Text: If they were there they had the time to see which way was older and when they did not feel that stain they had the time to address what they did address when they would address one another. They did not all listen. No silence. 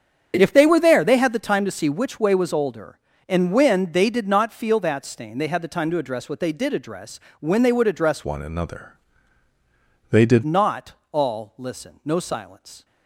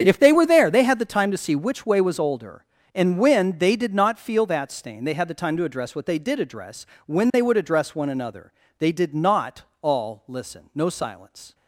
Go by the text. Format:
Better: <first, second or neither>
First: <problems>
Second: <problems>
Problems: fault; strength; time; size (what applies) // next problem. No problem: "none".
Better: second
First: starts louder than the rest; strong; until 1.4 s; 8 dB // pauses between "address" and "when"; slight; at 7.1 s; 0.20 s long // changes voice from "one" to "did"; from 8.2 to 10.4 s; 2.2 s long // pauses between "not" and "all"; slight; at 10.9 s; 0.18 s long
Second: starts louder than the rest; strong; until 1.0 s; 8 dB // pauses between "address" and "when"; slight; at 6.8 s; 0.20 s long // pauses between "not" and "all"; slight; at 9.6 s; 0.18 s long